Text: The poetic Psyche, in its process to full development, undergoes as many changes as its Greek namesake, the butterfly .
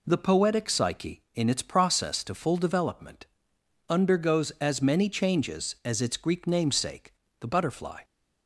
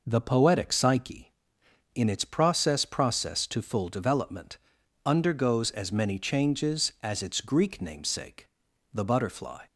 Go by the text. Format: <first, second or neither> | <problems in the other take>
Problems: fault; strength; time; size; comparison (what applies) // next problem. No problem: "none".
first | says "process" twice; at 2.8 s